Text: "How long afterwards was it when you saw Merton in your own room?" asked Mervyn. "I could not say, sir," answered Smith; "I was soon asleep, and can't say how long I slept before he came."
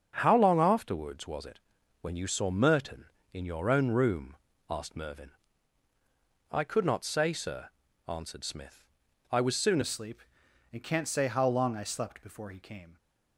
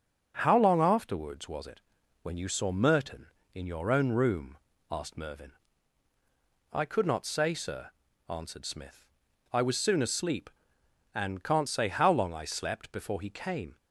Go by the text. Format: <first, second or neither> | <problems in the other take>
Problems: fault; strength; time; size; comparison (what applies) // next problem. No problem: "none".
second | starts louder than the rest; until 1.1 s; 7 dB // pauses between "it" and "when"; at 1.5 s; 0.42 s long; also in the second // changes voice at "asleep"; from 9.8 s on; 3.1 s long